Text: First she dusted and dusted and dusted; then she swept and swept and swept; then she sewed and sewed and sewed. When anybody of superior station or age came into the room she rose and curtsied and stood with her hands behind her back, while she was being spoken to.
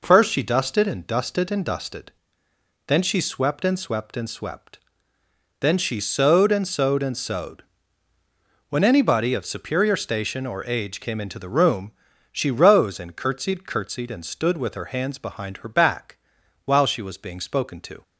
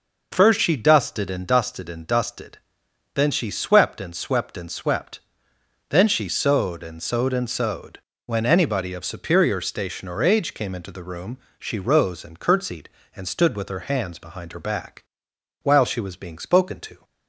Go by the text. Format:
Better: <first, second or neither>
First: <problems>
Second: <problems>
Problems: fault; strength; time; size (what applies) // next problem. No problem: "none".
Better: second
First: pauses between "room" and "she"; at 11.9 s; 0.40 s long // says "curtsied" twice; at 13.6 s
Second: pauses between "room" and "she"; slight; at 11.3 s; 0.22 s long